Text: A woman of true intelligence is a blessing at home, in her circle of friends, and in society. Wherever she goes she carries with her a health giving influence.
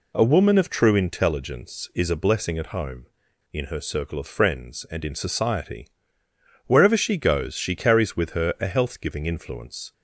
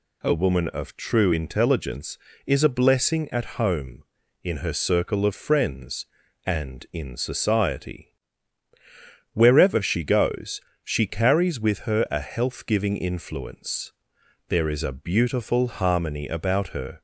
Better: first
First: none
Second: pauses between "goes" and "she"; slight; at 10.5 s; 0.24 s long // goes on to say "There is a beautiful harmony about her"; strong; from 14.4 s on; 2.5 s long

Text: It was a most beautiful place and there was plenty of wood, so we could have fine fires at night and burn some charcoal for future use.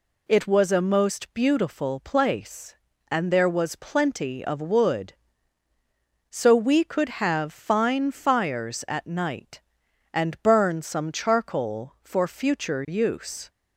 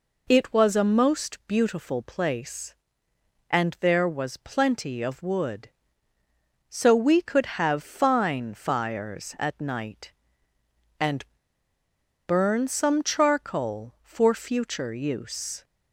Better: first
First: none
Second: pauses between "and" and "burn"; at 11.2 s; 1.0 s long

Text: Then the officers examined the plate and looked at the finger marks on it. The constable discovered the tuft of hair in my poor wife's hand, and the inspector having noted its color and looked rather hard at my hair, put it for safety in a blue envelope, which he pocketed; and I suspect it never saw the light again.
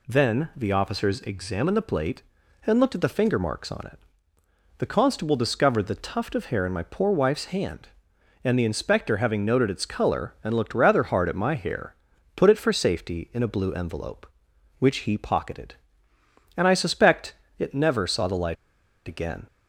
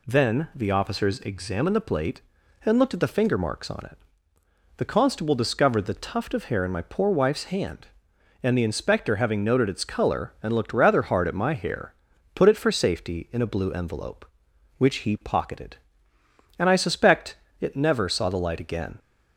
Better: second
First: pauses between "suspect" and "it"; slight; at 17.3 s; 0.24 s long // pauses between "light" and "again"; noticeable; at 18.5 s; 0.52 s long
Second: pauses between "suspect" and "it"; slight; at 17.3 s; 0.24 s long

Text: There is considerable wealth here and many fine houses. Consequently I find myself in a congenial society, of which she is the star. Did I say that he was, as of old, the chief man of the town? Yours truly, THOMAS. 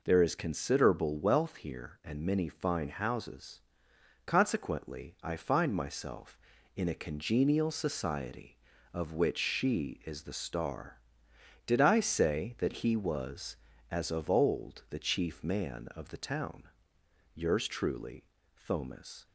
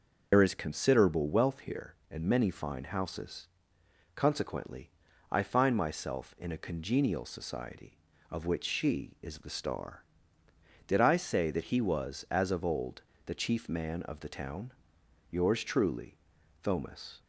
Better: first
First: none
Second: loses the start of "There"; at 0.3 s; 80 ms // pauses between "Consequently" and "I"; at 4.9 s; 0.40 s long

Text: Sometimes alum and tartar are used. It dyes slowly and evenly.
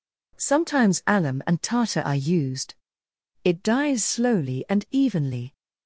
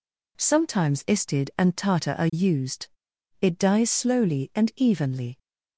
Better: first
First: none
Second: says "istid" for "alum"; at 1.0 s

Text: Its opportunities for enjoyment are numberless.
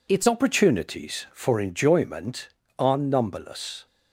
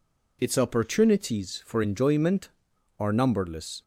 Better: second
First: changes voice at "opportunities"; from 0.2 s on; 3.6 s long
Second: none

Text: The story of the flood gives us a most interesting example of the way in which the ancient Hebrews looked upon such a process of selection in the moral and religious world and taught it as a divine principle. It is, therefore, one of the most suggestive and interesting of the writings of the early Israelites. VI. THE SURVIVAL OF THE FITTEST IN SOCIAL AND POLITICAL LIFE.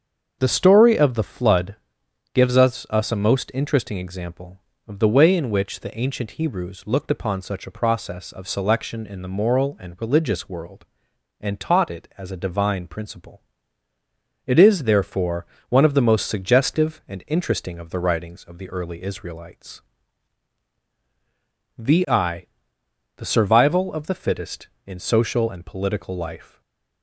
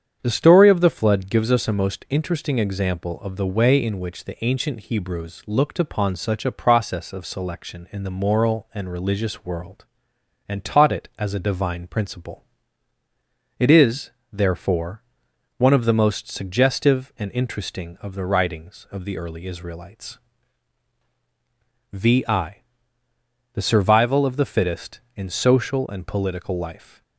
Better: second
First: starts louder than the rest; strong; until 1.4 s; 7 dB // pauses between "flood" and "gives"; noticeable; at 1.7 s; 0.58 s long // says "us" twice; at 2.8 s // stays silent after the last word; slight; from 26.4 s on; 0.6 s long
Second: starts louder than the rest; strong; until 1.2 s; 8 dB

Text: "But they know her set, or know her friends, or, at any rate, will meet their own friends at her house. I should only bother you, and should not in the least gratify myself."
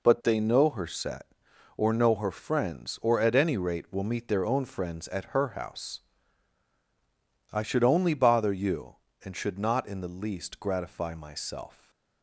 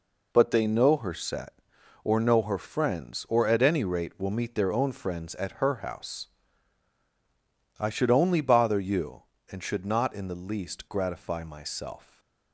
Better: neither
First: stays silent after the last word; slight; from 11.7 s on; 0.5 s long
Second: stays silent after the last word; slight; from 12.0 s on; 0.5 s long

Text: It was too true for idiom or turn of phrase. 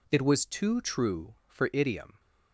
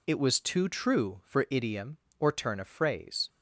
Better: second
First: stops before "or turn of phrase"; at 2.1 s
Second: none

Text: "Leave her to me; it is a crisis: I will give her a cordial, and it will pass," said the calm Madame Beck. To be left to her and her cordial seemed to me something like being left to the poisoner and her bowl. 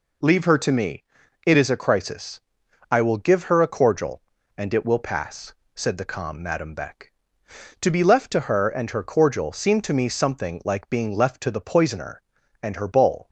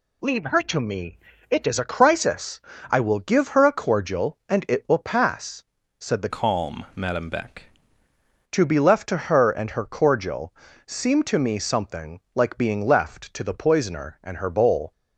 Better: first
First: none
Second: changes voice from "calm" to "Beck"; from 6.2 to 7.6 s; 1.4 s long // pauses between "cordial" and "seemed"; slight; at 10.5 s; 0.32 s long

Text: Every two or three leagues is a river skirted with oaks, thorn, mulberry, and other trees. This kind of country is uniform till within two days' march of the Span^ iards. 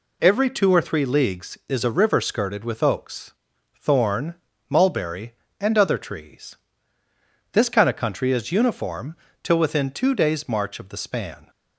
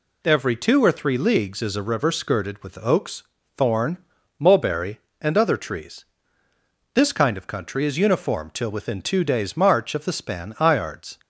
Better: second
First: pauses between "uniform" and "till"; slight; at 9.1 s; 0.26 s long // stops before "iards"; at 11.4 s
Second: none

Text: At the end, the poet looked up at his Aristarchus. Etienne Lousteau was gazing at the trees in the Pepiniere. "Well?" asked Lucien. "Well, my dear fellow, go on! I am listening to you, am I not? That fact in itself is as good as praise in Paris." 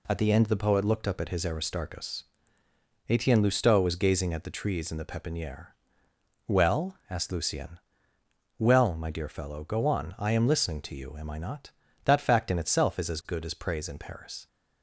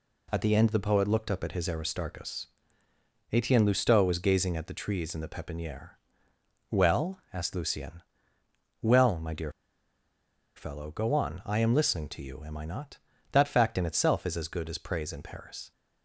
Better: first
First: none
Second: pauses between "dear" and "fellow"; at 9.5 s; 1.0 s long

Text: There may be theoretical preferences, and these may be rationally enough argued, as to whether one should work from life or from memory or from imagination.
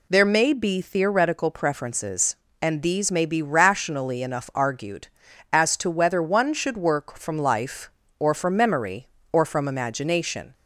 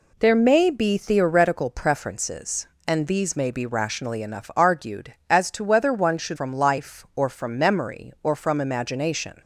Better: first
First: none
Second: skips "work"; at 6.3 s

